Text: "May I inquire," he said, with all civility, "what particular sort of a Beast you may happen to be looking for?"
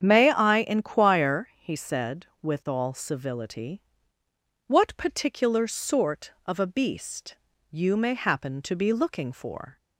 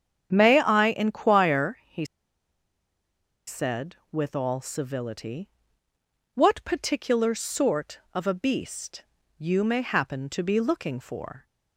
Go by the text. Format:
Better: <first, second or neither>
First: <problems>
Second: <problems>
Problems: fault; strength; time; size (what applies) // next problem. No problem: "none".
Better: first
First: starts louder than the rest; strong; until 1.0 s; 8 dB // pauses between "Beast" and "you"; slight; at 7.3 s; 0.34 s long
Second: starts louder than the rest; strong; until 1.3 s; 8 dB // pauses between "he" and "said"; strong; at 2.0 s; 1.4 s long // pauses between "Beast" and "you"; slight; at 9.0 s; 0.34 s long